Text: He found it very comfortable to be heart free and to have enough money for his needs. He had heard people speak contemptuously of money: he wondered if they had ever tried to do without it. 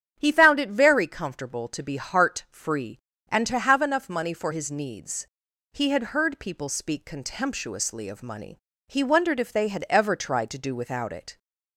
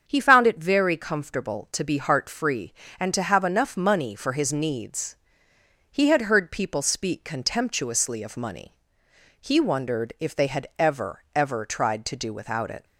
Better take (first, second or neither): first